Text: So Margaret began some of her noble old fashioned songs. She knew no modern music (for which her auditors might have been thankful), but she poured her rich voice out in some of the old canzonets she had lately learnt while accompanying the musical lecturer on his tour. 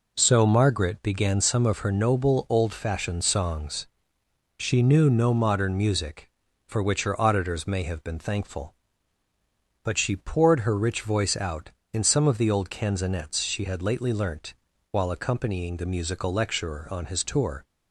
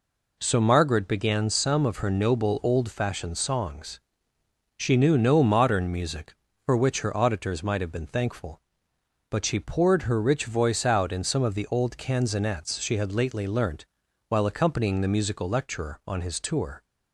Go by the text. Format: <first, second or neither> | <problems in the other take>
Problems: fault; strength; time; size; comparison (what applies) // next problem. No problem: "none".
second | says "may" for "might"; at 7.6 s // pauses between "learnt" and "while"; at 14.5 s; 0.38 s long; also in the second